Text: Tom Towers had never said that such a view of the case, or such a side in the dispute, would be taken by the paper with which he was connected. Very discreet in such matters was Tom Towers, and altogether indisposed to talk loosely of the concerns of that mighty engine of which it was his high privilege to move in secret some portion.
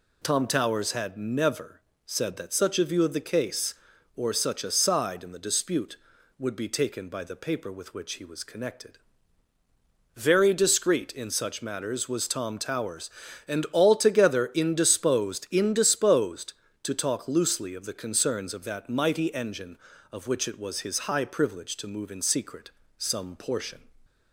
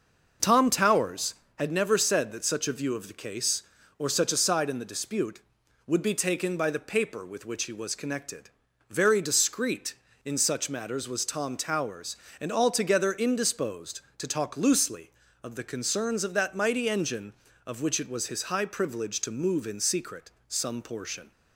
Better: second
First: pauses between "never" and "said"; slight; at 1.8 s; 0.26 s long // says "indisposed" twice; at 15.5 s // pauses between "secret" and "some"; slight; at 22.7 s; 0.26 s long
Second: pauses between "secret" and "some"; slight; at 20.3 s; 0.16 s long

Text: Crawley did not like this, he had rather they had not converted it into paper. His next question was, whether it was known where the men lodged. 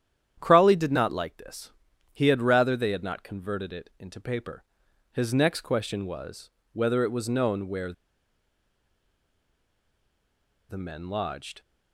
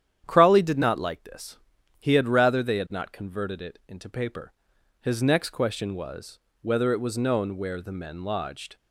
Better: second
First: starts louder than the rest; strong; until 1.4 s; 10 dB // pauses between "where" and "the"; strong; at 7.9 s; 2.7 s long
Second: starts louder than the rest; strong; until 1.2 s; 10 dB

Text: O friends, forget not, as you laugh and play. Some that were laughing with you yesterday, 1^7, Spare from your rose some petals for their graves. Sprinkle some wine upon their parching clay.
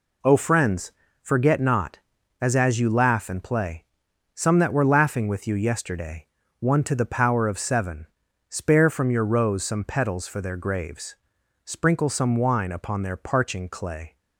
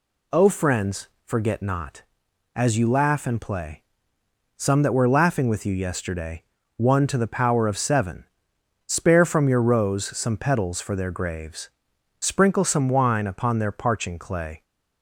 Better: second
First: says "as" twice; at 2.5 s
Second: none

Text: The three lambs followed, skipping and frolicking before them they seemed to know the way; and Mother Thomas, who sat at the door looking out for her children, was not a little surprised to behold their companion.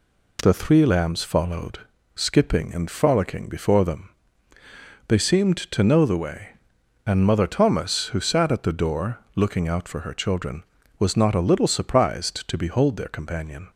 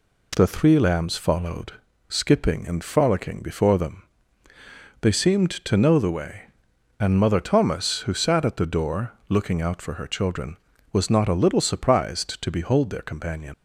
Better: first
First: pauses between "them" and "they"; at 4.0 s; 1.0 s long // pauses between "door" and "looking"; slight; at 9.1 s; 0.16 s long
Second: pauses between "them" and "they"; at 4.0 s; 1.0 s long // pauses between "door" and "looking"; slight; at 9.1 s; 0.16 s long // leaves "companion" unfinished; at 13.5 s; 100 ms

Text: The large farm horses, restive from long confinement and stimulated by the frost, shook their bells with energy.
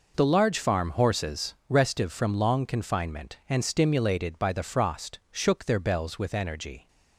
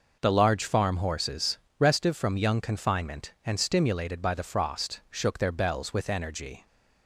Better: first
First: none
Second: says "young" for "long"; at 2.3 s

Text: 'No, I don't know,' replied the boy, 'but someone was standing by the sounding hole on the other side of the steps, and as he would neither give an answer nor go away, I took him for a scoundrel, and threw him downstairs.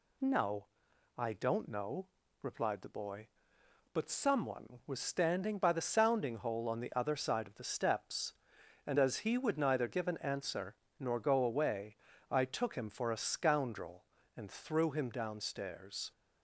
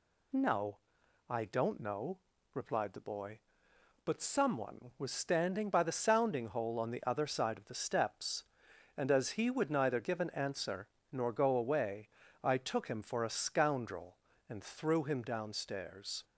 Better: neither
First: pauses between "answer" and "nor"; slight; at 10.7 s; 0.24 s long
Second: pauses between "answer" and "nor"; slight; at 10.8 s; 0.24 s long

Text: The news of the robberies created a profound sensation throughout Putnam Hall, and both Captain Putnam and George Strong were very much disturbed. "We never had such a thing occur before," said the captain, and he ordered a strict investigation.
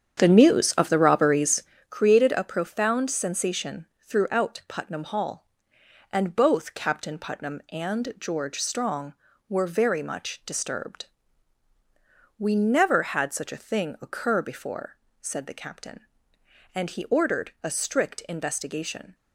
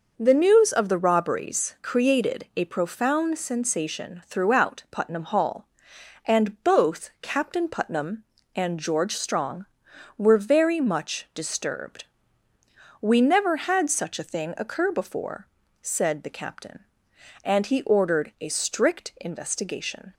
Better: second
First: starts louder than the rest; strong; until 1.9 s; 8.5 dB // pauses between "robberies" and "created"; slight; at 1.6 s; 0.28 s long // pauses between "sensation" and "throughout"; slight; at 3.8 s; 0.16 s long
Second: none

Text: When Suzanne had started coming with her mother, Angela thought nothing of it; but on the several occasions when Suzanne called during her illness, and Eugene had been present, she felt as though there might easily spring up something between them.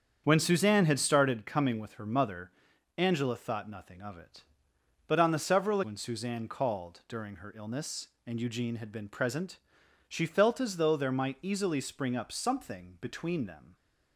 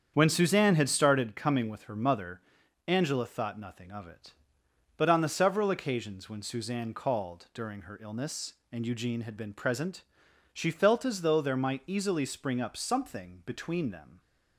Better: second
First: starts louder than the rest; strong; until 1.2 s; 7.5 dB // skips "occasions"; at 5.8 s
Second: starts louder than the rest; strong; until 1.1 s; 8 dB

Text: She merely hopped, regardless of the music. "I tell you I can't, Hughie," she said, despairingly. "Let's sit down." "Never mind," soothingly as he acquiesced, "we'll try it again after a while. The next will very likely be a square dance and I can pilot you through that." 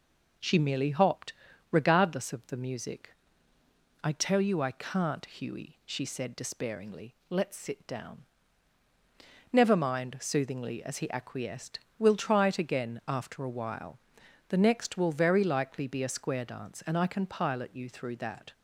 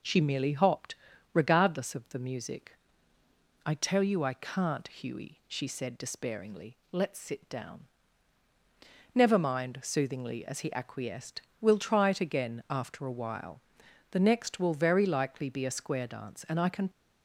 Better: first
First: none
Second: stops before "pilot you through that"; at 16.9 s

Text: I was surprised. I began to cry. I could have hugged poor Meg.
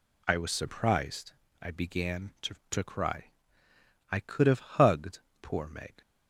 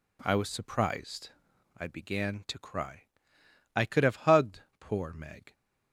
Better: second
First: says "to" twice; at 2.7 s // pauses between "hugged" and "poor"; slight; at 5.1 s; 0.22 s long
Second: pauses between "hugged" and "poor"; slight; at 4.6 s; 0.18 s long

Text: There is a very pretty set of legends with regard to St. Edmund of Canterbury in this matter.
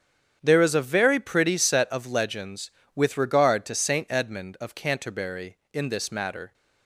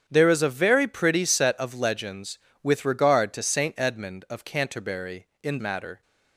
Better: first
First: starts louder than the rest; strong; until 1.4 s; 8.5 dB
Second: starts louder than the rest; strong; until 1.0 s; 8.5 dB // skips "this"; at 5.5 s

